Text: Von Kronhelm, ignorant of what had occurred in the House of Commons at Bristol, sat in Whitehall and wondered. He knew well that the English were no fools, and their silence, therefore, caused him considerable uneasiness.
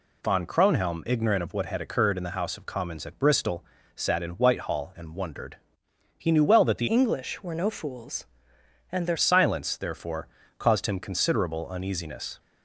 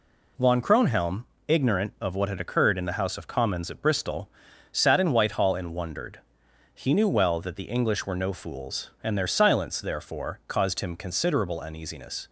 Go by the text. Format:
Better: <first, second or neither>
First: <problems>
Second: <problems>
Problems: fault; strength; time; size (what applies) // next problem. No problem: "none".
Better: second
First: changes voice from "English" to "their"; from 6.8 to 9.1 s; 2.3 s long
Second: none